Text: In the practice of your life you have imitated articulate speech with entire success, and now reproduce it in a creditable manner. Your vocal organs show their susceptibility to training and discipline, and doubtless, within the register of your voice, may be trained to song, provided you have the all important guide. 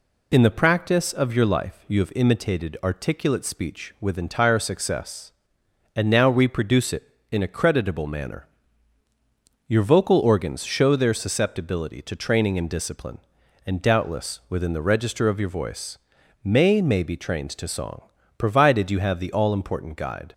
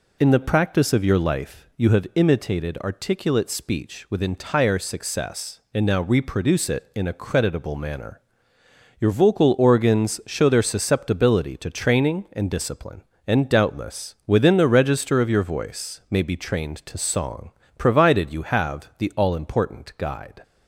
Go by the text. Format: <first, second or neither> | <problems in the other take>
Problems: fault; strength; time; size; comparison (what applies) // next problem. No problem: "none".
second | says "may" twice; at 16.8 s